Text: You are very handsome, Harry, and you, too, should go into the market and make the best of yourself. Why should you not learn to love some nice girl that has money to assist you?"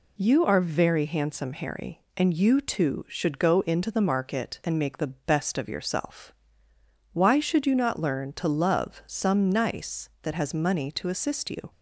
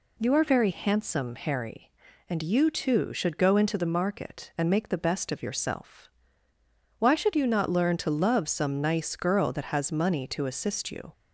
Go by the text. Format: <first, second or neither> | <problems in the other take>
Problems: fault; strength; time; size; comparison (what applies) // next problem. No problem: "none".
second | skips "girl"; at 10.1 s